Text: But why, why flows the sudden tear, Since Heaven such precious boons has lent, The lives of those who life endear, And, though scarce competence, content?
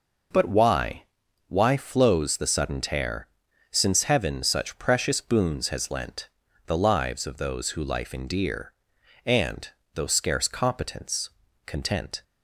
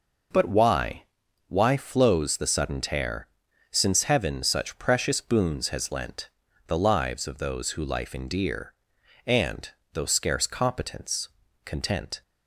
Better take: neither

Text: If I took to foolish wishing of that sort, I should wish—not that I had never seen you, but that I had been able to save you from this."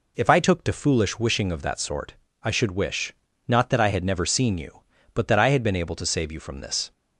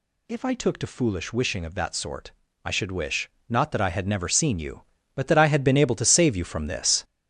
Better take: first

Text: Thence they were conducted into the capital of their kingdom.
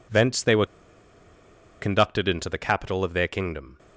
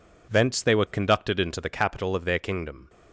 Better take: second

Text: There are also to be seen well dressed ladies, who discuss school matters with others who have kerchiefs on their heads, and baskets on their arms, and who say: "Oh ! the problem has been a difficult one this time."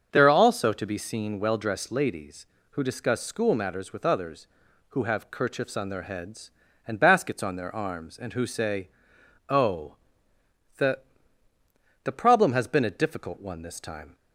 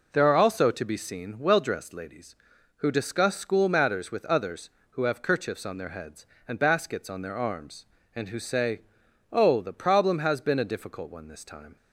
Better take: second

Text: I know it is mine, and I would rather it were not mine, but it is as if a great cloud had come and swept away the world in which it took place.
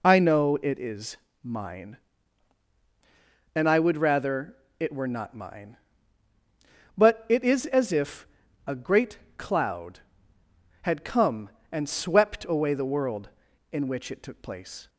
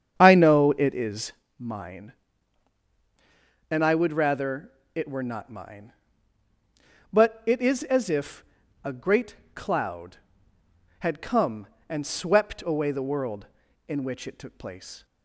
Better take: first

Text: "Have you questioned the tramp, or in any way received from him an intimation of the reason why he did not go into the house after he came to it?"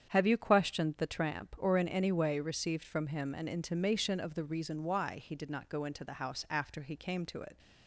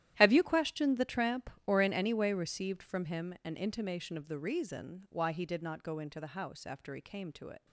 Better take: first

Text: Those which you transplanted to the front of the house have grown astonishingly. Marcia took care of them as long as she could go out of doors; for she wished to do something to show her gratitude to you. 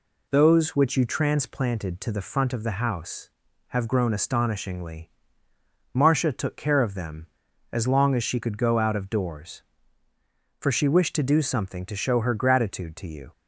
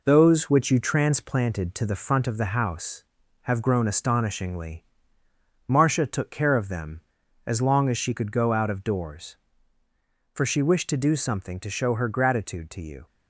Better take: first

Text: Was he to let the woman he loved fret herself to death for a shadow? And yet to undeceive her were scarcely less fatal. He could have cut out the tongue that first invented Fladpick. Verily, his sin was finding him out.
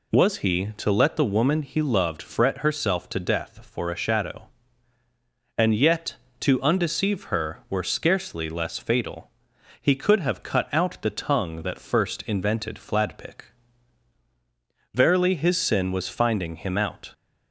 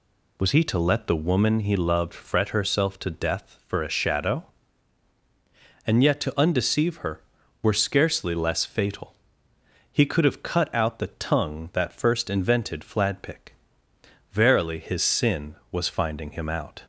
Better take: neither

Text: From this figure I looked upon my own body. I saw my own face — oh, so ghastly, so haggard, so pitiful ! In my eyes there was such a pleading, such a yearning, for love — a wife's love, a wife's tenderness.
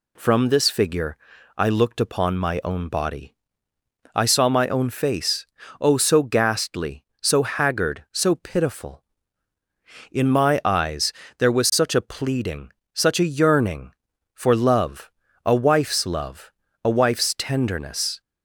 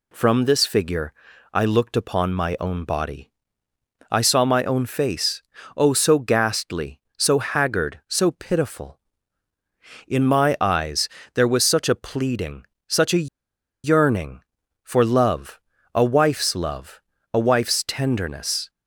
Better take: first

